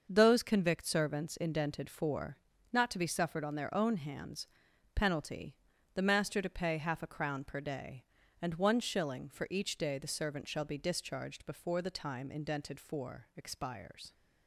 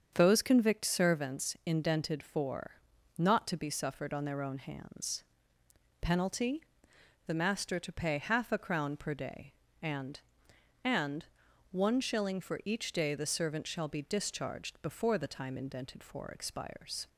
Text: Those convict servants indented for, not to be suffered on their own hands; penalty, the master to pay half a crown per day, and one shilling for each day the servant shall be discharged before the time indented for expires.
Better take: first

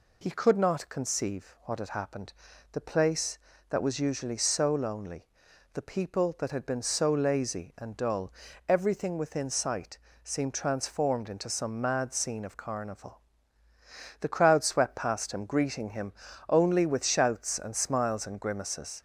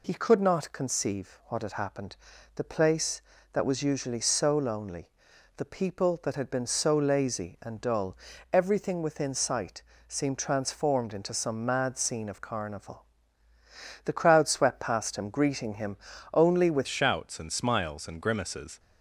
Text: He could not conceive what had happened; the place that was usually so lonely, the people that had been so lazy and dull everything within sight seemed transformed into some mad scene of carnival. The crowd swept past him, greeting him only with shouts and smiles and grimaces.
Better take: first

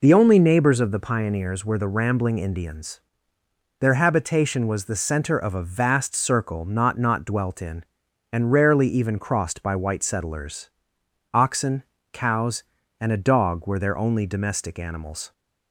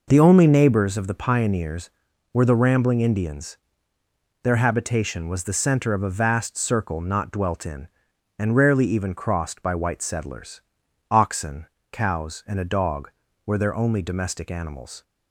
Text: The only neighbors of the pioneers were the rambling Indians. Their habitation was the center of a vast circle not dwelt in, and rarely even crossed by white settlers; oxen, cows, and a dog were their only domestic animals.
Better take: second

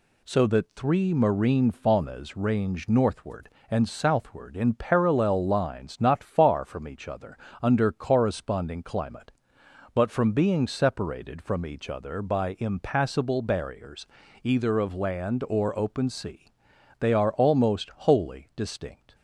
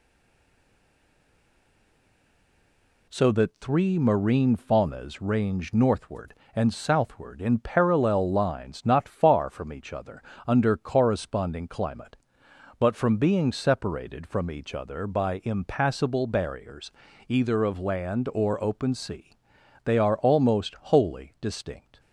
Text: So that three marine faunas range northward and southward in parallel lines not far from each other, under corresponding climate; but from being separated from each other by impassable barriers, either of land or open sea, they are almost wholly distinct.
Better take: first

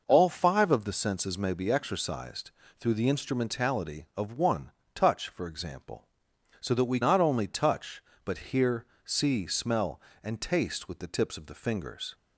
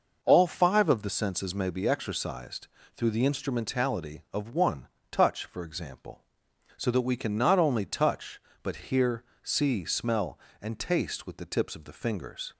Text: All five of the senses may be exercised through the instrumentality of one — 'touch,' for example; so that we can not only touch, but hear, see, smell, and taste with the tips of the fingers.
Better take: second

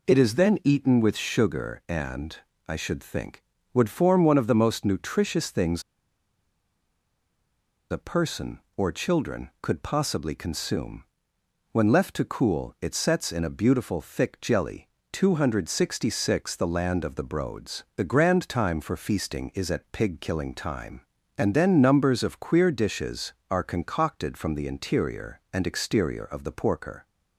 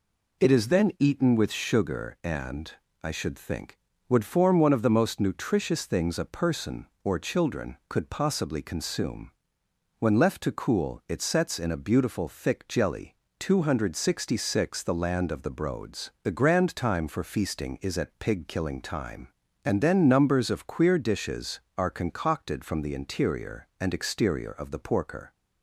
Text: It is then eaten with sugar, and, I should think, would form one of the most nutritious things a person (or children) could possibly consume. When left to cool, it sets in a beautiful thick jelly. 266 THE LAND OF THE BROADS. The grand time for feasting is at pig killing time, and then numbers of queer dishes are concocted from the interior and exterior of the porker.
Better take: second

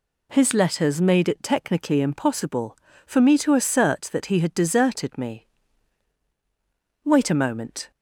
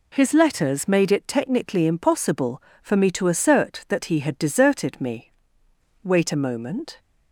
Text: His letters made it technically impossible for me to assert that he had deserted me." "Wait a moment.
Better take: neither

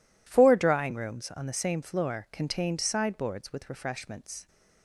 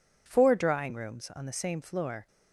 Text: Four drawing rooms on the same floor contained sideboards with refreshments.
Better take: first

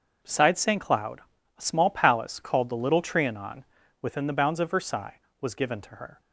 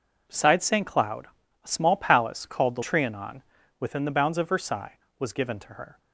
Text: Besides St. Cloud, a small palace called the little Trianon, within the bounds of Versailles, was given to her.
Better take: first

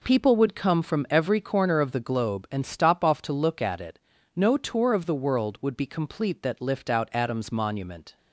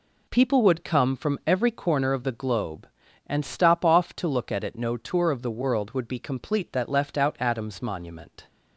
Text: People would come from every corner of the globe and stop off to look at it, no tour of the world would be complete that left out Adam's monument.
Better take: second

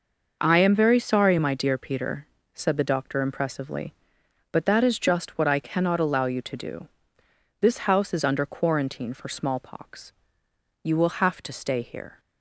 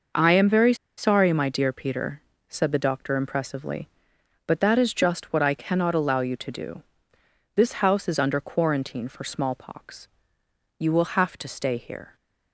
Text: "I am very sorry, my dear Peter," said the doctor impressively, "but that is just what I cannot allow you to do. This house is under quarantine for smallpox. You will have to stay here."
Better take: first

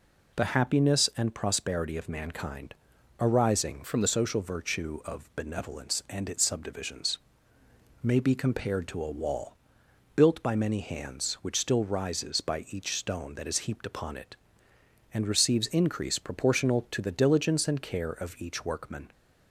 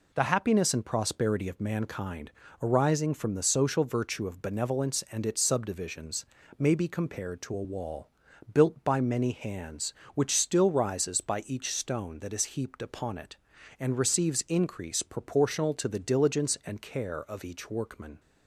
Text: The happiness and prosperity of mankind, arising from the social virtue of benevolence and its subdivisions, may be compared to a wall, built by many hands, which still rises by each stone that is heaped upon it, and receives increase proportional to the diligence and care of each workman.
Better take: second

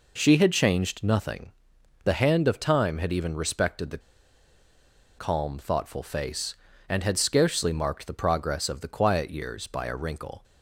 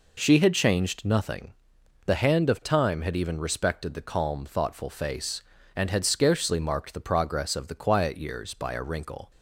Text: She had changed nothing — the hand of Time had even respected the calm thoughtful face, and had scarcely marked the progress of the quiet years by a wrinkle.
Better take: second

